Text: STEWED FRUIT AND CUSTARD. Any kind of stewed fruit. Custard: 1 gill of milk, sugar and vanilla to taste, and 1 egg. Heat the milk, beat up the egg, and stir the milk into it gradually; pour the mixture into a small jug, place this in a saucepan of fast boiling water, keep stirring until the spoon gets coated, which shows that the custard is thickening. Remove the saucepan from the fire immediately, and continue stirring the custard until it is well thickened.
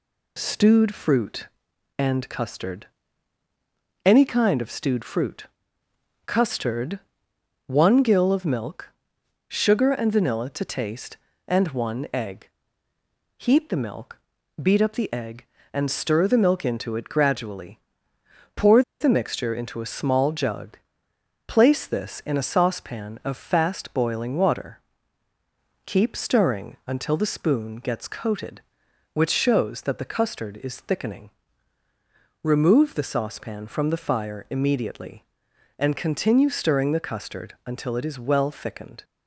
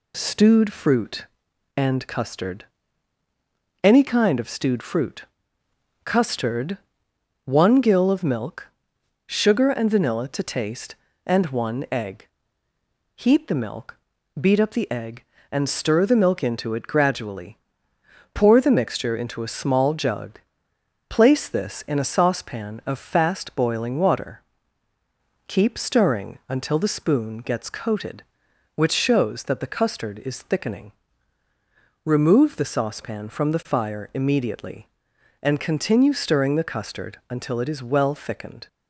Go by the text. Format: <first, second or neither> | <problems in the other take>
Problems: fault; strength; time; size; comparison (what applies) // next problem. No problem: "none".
second | pauses between "pour" and "the"; slight; at 18.8 s; 0.17 s long